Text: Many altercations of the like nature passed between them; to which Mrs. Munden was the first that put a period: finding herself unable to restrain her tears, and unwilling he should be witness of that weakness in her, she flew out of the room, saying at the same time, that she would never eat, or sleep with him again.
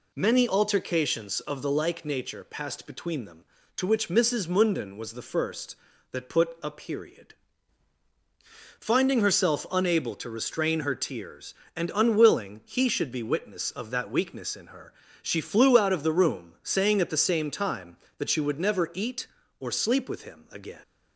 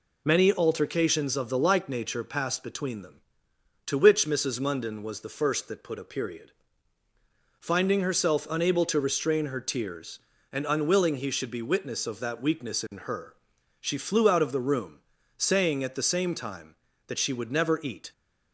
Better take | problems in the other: first | stops before "or sleep with him again"; at 18.1 s

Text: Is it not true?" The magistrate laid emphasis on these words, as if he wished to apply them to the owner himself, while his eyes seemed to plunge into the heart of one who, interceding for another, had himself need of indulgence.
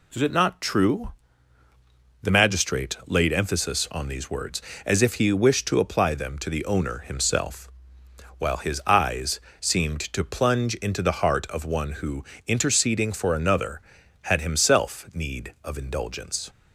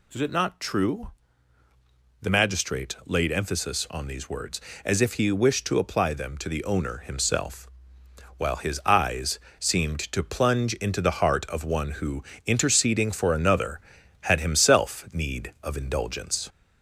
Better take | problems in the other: first | gets louder; slight; throughout; 2 dB // pauses between "eyes" and "seemed"; slight; at 9.3 s; 0.20 s long; slight in the first

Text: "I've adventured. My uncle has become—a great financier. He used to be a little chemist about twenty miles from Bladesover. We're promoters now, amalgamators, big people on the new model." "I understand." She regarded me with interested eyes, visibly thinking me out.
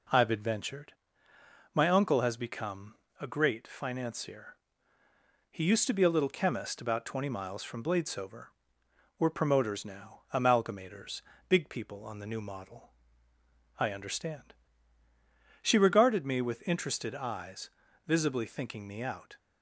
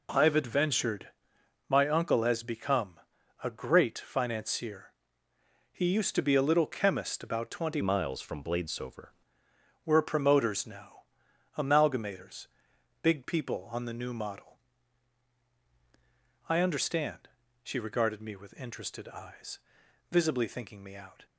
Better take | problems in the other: first | changes voice from "miles" to "Bladesover"; from 7.8 to 9.0 s; 1.2 s long

